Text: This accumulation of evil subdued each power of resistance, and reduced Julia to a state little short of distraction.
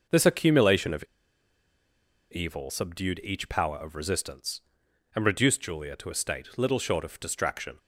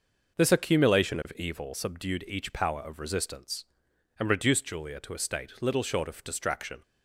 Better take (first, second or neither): second